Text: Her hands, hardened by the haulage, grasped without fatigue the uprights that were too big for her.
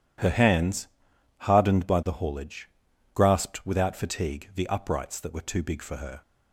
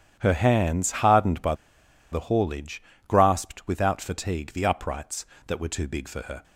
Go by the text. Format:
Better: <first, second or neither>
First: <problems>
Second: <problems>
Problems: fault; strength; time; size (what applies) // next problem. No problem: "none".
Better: first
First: none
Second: starts louder than the rest; strong; until 1.2 s; 10 dB // pauses between "by" and "the"; noticeable; at 1.5 s; 0.58 s long